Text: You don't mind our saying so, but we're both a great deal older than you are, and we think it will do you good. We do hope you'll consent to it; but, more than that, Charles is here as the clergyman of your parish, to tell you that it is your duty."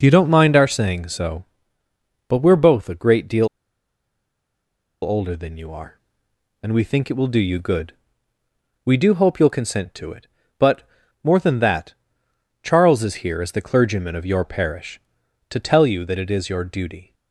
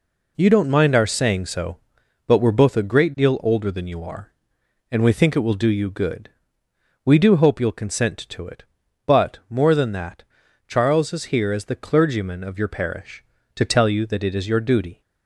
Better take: second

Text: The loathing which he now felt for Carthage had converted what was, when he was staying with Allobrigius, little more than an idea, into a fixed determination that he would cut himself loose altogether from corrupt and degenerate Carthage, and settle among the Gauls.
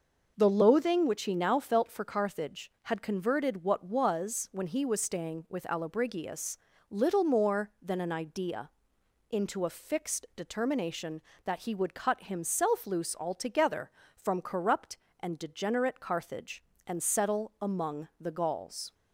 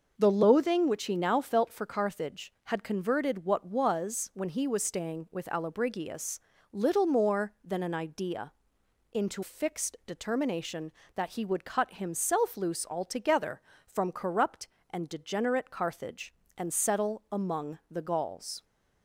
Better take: first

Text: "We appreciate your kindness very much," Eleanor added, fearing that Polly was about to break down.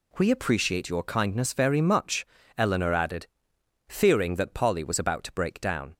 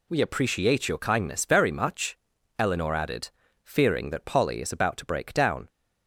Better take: first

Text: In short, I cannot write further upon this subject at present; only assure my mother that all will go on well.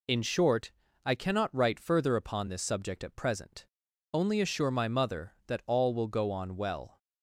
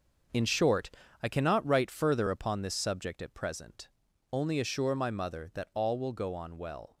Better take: first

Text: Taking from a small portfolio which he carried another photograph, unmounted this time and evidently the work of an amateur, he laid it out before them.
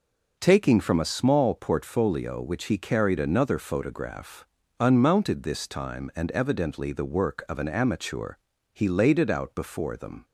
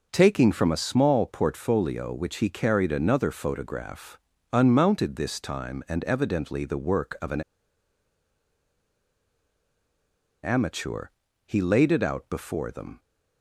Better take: first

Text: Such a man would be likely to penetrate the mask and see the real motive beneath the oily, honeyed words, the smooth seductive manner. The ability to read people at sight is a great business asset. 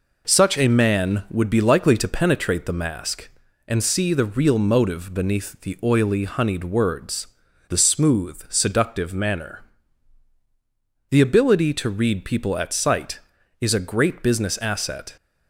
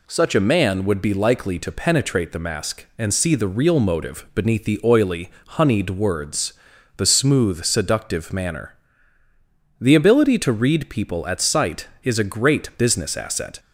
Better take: neither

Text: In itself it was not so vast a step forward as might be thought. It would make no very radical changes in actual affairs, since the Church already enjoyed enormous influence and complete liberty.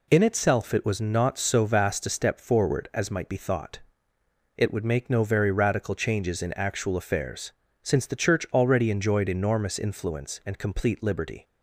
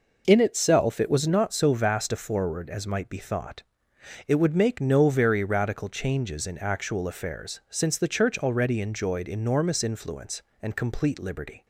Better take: first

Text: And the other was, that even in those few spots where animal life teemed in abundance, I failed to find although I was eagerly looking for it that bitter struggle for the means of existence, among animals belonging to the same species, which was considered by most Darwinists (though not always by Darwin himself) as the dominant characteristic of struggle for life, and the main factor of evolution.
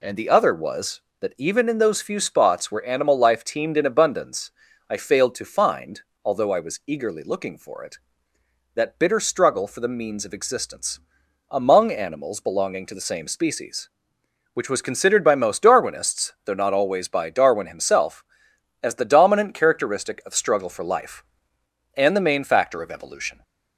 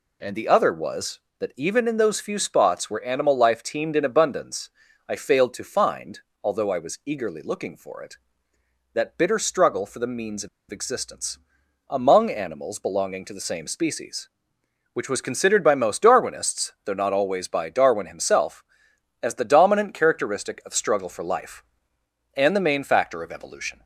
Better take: first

